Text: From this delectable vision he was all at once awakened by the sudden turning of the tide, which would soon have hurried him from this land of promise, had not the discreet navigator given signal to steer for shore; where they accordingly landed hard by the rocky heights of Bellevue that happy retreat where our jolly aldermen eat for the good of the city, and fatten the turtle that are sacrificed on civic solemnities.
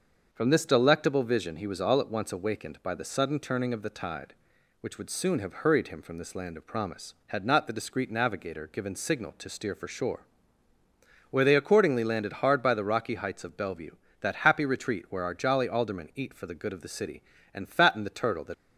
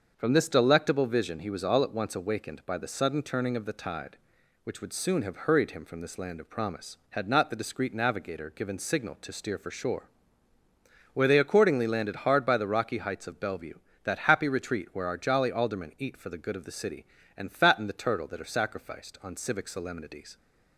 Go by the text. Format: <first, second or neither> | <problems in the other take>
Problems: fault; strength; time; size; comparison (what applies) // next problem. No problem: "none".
second | starts louder than the rest; until 1.3 s; 6.5 dB; also in the second // stops before "are sacrificed on civic solemnities"; at 18.5 s